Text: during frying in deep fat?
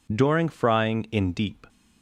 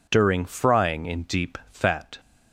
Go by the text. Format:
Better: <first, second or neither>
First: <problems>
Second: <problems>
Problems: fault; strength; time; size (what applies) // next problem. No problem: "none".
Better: second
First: stops before "fat"; at 1.6 s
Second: none